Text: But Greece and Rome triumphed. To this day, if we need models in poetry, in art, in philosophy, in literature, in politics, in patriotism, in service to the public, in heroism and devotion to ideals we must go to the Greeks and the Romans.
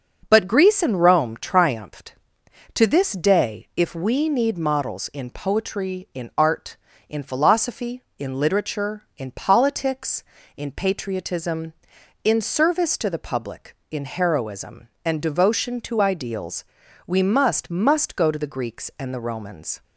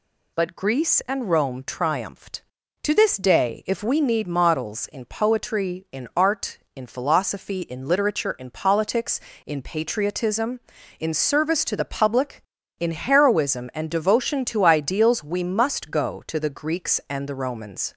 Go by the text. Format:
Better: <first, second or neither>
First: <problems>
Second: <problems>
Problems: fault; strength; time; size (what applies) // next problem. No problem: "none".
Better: second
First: starts louder than the rest; noticeable; until 1.3 s; 6 dB // pauses between "ideals" and "we"; at 16.6 s; 0.42 s long // says "must" twice; at 17.6 s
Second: none